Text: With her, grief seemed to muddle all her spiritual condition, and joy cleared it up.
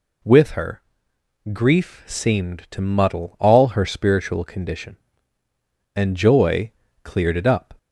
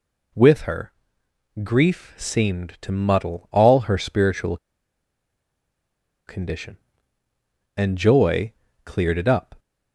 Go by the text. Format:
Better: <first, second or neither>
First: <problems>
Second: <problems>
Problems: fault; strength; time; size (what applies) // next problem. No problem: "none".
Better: first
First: pauses between "joy" and "cleared"; slight; at 6.7 s; 0.32 s long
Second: pauses between "spiritual" and "condition"; strong; at 4.5 s; 1.7 s long // pauses between "joy" and "cleared"; slight; at 8.5 s; 0.32 s long